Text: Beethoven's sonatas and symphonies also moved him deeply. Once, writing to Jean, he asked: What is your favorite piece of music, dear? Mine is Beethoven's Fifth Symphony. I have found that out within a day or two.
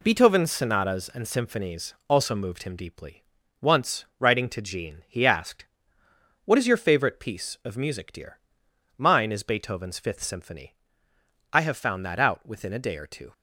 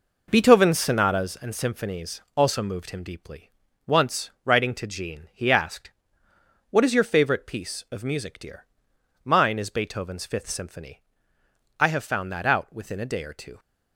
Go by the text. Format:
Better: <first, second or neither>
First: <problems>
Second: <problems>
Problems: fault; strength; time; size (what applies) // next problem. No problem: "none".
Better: first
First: pauses between "symphonies" and "also"; slight; at 1.9 s; 0.16 s long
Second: starts louder than the rest; noticeable; until 1.3 s; 5 dB // pauses between "symphonies" and "also"; slight; at 2.2 s; 0.16 s long